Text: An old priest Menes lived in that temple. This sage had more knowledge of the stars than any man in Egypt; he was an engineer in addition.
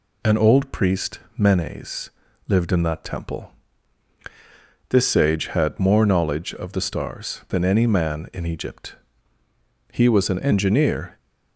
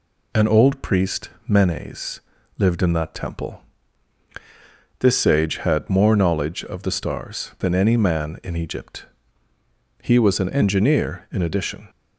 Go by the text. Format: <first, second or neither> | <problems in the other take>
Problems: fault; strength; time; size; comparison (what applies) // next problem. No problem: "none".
second | pauses between "priest" and "Menes"; slight; at 1.1 s; 0.18 s long; slight in the second // pauses between "Menes" and "lived"; slight; at 2.1 s; 0.36 s long; slight in the second // stops before "in addition"; at 11.1 s